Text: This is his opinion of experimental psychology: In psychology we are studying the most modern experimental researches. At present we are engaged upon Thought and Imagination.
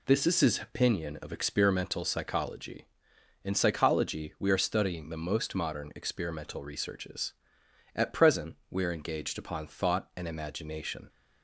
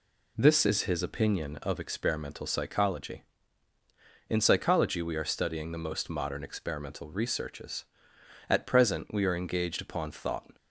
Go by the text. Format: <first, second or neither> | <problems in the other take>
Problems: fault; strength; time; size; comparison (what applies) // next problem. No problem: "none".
first | stops before "and Imagination"; at 10.5 s